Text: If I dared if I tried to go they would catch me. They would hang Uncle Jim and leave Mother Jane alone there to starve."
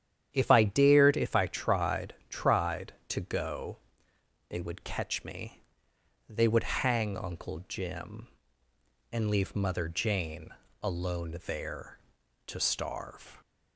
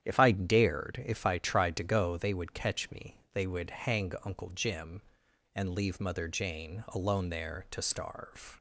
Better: second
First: starts louder than the rest; strong; until 1.3 s; 9.5 dB // says "tried" twice; at 2.2 s // pauses between "go" and "they"; noticeable; at 3.7 s; 0.72 s long // pauses between "Jane" and "alone"; slight; at 10.4 s; 0.34 s long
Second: starts louder than the rest; strong; until 1.0 s; 10 dB

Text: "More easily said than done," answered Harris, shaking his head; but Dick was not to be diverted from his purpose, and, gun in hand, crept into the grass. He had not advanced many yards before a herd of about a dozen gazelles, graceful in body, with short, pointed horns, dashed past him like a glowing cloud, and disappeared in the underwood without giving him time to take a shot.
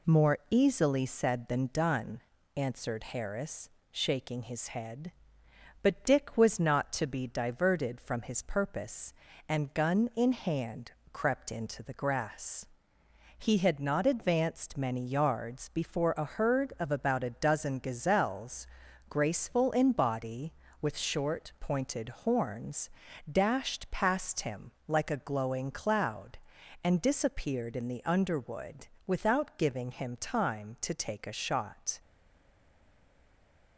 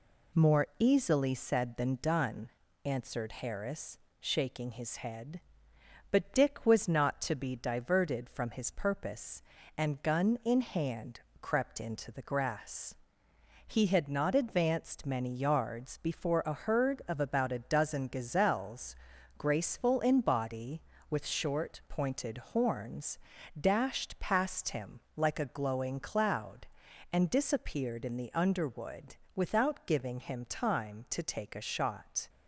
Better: second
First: pauses between "underwood" and "without"; slight; at 28.8 s; 0.18 s long // stays silent after the last word; noticeable; from 31.9 s on; 1.8 s long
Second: pauses between "underwood" and "without"; slight; at 29.1 s; 0.18 s long

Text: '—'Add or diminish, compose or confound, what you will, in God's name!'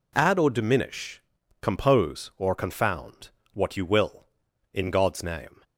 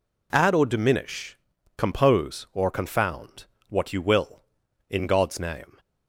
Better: neither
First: none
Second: none

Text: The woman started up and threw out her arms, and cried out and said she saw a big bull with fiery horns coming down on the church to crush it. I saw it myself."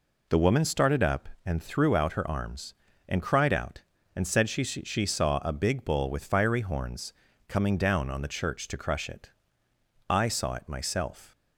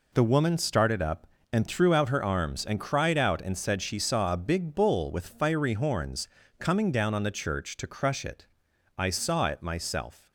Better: second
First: says "she" twice; at 4.6 s // pauses between "horns" and "coming"; slight; at 7.1 s; 0.34 s long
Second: pauses between "horns" and "coming"; slight; at 6.2 s; 0.32 s long

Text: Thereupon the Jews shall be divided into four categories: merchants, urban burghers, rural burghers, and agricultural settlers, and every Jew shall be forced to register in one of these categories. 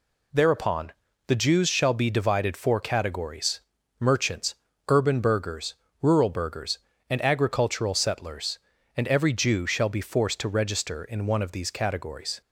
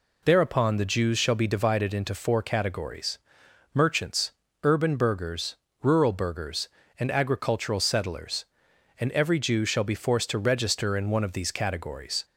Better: second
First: pauses between "Thereupon" and "the"; slight; at 0.9 s; 0.34 s long // skips "into"; at 2.5 s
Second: none

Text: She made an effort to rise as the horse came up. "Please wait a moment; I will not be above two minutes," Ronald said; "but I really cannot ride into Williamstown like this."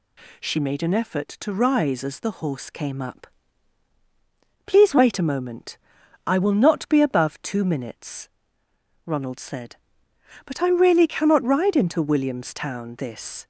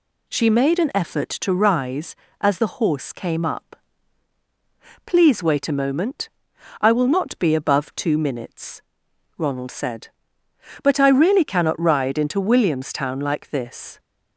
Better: second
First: skips "like"; at 12.9 s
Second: none

